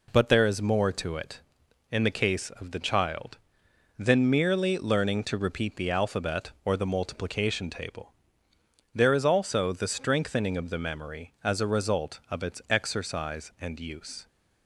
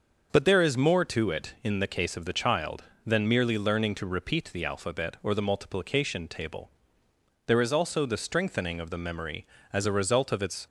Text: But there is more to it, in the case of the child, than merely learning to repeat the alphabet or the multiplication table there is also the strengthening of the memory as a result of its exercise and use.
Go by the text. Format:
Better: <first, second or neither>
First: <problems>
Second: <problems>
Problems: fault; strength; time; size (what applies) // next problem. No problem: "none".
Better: first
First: pauses between "table" and "there"; noticeable; at 8.1 s; 0.82 s long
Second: starts louder than the rest; until 1.3 s; 6 dB // pauses between "table" and "there"; noticeable; at 6.7 s; 0.76 s long // stops before "exercise and use"; at 10.6 s